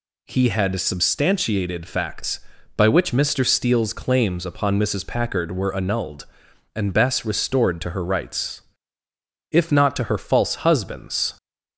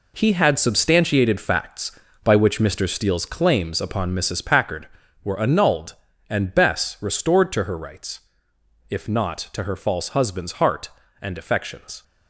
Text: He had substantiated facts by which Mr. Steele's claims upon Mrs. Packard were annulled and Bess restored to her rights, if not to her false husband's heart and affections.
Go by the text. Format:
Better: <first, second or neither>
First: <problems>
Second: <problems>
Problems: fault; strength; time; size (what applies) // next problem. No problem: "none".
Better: second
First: stops before "heart and affections"; at 11.3 s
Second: none